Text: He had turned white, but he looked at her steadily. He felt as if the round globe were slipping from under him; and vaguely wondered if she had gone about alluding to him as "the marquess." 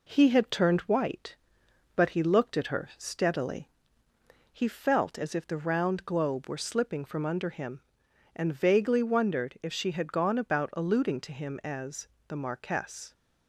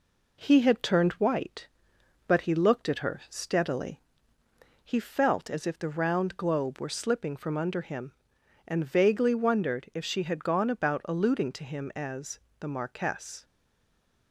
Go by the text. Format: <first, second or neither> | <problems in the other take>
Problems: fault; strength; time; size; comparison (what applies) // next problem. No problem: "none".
first | pauses between "as" and "the"; slight; at 12.3 s; 0.22 s long; slight in the first // stays silent after the last word; slight; from 13.4 s on; 0.9 s long